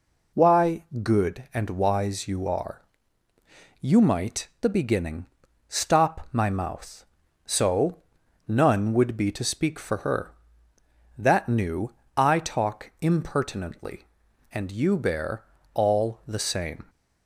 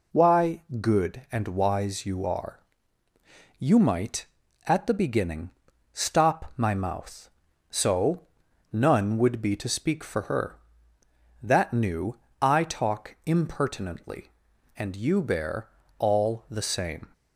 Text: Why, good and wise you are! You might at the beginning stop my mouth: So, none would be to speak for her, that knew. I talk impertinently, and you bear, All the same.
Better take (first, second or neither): second